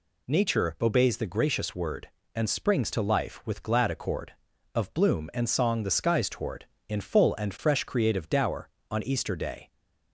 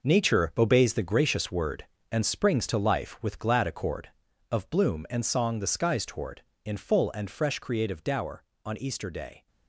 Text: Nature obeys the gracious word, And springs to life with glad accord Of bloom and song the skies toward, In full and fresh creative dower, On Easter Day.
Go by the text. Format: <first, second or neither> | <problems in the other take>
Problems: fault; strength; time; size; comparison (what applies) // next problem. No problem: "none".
first | gets quieter; strong; throughout; 11.5 dB